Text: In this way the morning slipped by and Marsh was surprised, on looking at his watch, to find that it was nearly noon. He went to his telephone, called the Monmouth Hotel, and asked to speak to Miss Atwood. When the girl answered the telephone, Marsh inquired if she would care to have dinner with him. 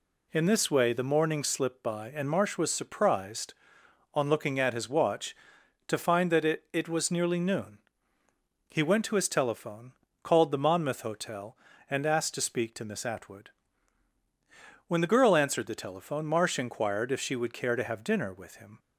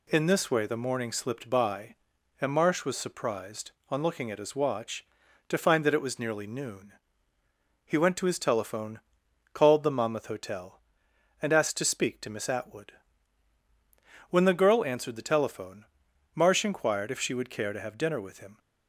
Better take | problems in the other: second | says "it" twice; at 6.7 s

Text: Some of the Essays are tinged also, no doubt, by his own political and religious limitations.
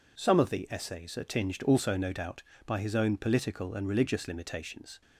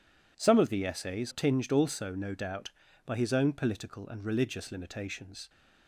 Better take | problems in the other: first | skips "are"; at 1.3 s

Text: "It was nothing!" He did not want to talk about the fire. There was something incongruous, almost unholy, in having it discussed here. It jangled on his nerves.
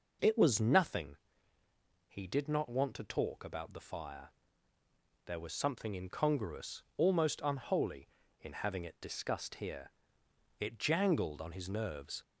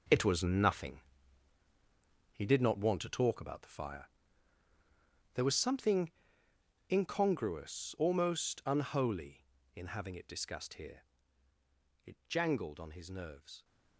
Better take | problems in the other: first | gets quieter; strong; throughout; 10.5 dB // pauses between "something" and "incongruous"; noticeable; at 6.1 s; 0.78 s long

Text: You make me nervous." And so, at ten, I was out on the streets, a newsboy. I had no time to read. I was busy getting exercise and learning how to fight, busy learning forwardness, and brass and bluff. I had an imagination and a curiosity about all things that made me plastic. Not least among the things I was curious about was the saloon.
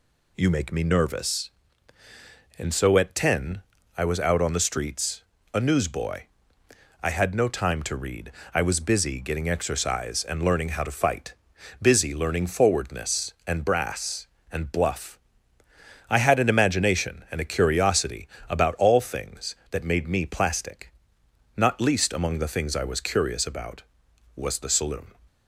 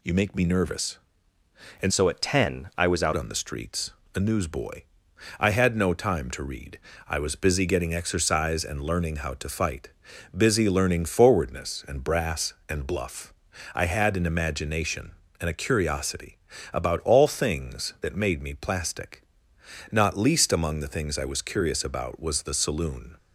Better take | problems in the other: first | changes voice from "so" to "out"; from 1.9 to 3.1 s; 1.2 s long // pauses between "curiosity" and "about"; slight; at 16.3 s; 0.36 s long; slight in the first

